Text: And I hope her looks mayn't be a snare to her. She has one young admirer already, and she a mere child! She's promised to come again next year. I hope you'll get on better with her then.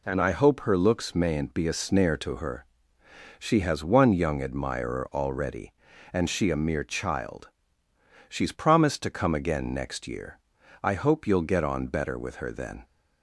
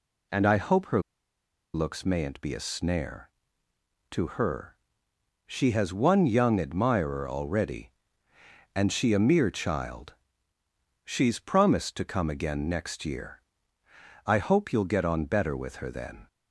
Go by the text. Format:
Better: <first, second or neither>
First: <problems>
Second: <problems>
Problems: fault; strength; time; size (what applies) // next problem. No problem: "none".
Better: first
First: none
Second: pauses between "her" and "looks"; noticeable; at 1.0 s; 0.72 s long